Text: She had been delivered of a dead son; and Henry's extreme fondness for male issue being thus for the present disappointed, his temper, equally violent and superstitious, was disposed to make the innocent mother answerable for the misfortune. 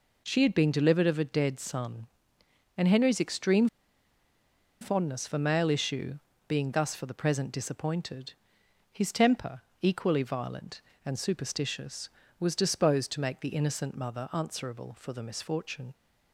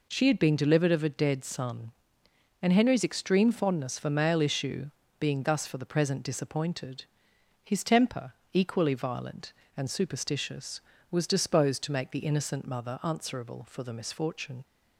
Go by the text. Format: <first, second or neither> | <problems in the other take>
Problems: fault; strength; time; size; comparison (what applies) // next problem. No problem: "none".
second | pauses between "extreme" and "fondness"; at 3.6 s; 1.1 s long // pauses between "issue" and "being"; slight; at 6.1 s; 0.30 s long; slight in the second